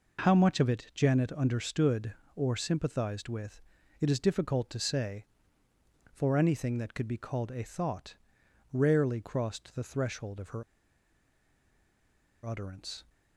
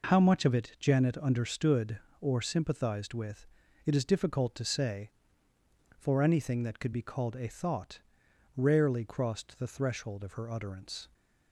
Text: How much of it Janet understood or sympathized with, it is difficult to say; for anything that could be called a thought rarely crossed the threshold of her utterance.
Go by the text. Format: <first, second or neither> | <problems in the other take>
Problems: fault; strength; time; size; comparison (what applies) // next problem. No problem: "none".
second | pauses between "thought" and "rarely"; noticeable; at 8.1 s; 0.58 s long; noticeable in the second // pauses between "her" and "utterance"; strong; at 10.6 s; 1.8 s long